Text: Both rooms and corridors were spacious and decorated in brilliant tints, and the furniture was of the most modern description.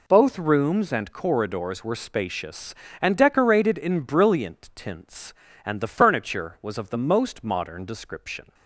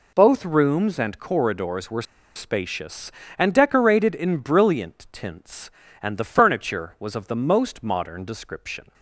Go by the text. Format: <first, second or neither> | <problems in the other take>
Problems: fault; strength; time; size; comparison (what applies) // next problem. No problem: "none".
first | pauses between "were" and "spacious"; slight; at 2.0 s; 0.32 s long